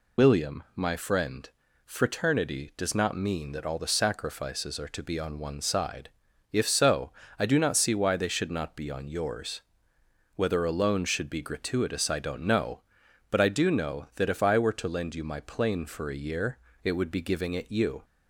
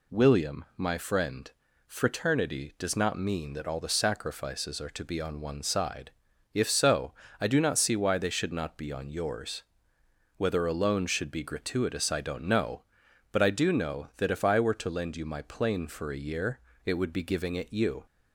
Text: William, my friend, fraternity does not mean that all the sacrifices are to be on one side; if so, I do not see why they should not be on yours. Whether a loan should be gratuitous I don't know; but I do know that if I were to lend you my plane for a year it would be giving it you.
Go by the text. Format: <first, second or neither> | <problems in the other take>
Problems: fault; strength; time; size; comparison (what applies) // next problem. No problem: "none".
second | loses the start of "William"; at 0.1 s; 85 ms // pauses between "year" and "it"; slight; at 16.5 s; 0.26 s long; slight in the second